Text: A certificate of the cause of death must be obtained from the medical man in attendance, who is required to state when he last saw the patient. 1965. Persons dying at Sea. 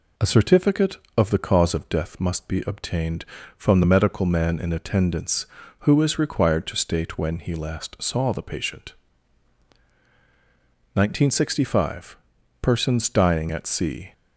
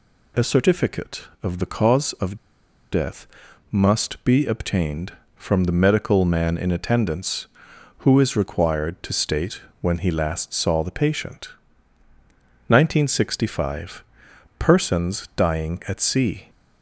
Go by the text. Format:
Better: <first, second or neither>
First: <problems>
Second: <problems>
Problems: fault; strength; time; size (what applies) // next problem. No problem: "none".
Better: first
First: none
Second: pauses between "of" and "death"; noticeable; at 2.3 s; 0.56 s long // pauses between "death" and "must"; at 3.2 s; 0.42 s long // pauses between "state" and "when"; slight; at 9.6 s; 0.20 s long